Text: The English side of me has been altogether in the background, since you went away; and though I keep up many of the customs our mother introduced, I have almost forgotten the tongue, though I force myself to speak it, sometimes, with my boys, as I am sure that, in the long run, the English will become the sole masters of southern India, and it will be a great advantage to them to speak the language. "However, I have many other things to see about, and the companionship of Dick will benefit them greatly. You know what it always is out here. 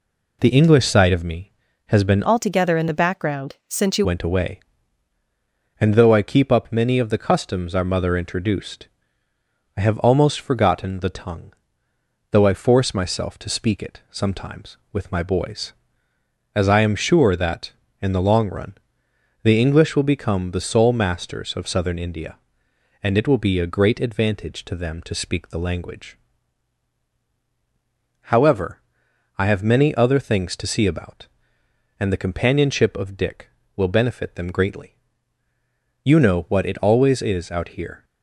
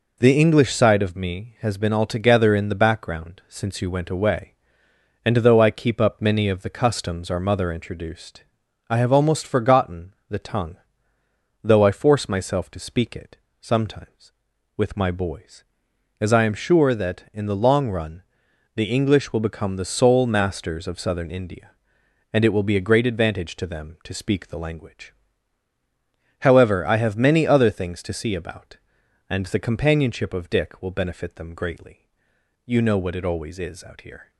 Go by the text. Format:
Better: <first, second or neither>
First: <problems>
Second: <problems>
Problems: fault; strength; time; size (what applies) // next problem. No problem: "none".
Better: second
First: changes voice from "altogether" to "you"; from 2.2 to 4.0 s; 1.8 s long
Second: none